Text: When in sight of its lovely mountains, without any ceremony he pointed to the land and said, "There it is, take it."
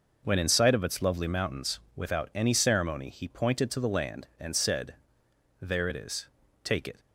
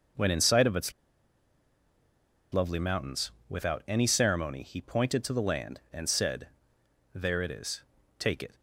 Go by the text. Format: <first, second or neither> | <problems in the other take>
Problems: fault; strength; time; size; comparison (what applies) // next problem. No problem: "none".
first | pauses between "its" and "lovely"; strong; at 0.9 s; 1.5 s long